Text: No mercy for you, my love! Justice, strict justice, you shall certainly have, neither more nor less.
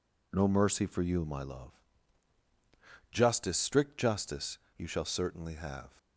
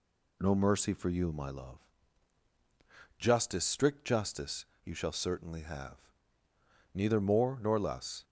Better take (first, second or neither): second